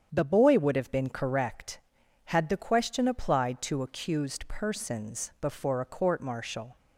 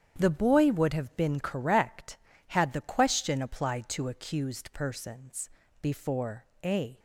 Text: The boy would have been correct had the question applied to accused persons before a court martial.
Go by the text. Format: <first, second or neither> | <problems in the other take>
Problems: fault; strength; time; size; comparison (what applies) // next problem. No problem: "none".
first | starts louder than the rest; strong; until 1.1 s; 8.5 dB; strong in the first // pauses between "persons" and "before"; slight; at 5.5 s; 0.32 s long // pauses between "before" and "a"; slight; at 6.4 s; 0.18 s long // stops before "court martial"; at 6.9 s